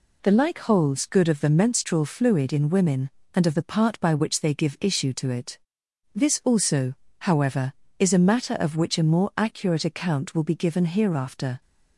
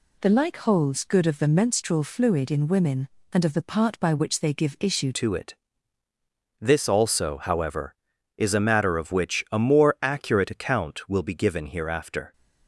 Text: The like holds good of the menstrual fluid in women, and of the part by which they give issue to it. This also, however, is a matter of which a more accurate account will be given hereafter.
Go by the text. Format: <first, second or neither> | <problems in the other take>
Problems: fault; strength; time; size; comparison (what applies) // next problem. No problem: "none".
first | changes voice at "to"; from 5.1 s on; 7.2 s long